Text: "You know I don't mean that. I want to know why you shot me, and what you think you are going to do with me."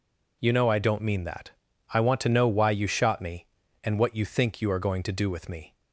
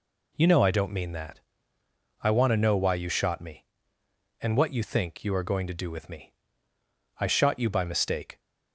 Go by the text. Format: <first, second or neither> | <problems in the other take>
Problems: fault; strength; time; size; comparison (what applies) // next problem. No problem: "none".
first | goes on to say "I shot you by mistake"; noticeable; from 7.2 s on; 1.1 s long